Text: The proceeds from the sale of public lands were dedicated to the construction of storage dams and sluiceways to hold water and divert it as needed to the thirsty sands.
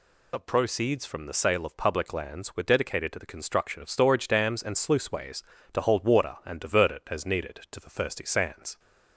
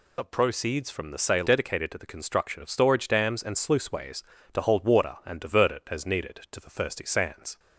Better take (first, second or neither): first